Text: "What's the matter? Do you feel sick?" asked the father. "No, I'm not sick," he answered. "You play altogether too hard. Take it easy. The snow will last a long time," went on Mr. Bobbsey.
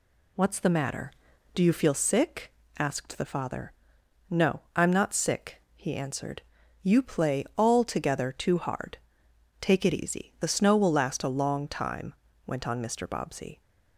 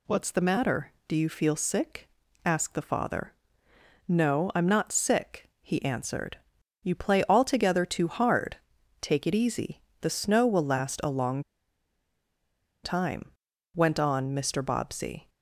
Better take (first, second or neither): first